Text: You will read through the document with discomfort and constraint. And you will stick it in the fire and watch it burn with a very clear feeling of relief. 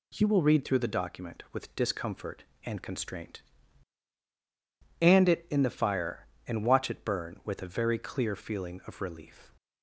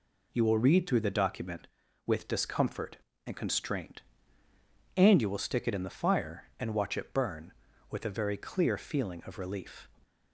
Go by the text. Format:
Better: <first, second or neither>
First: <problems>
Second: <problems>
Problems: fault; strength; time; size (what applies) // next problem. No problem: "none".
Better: second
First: skips "you will stick"; at 5.2 s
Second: none